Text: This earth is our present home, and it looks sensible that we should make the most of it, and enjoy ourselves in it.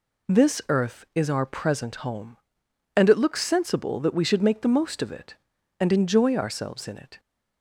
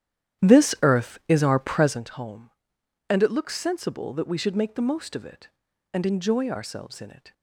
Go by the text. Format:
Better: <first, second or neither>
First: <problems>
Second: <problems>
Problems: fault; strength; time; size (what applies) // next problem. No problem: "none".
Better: first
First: none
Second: starts louder than the rest; strong; until 2.1 s; 10.5 dB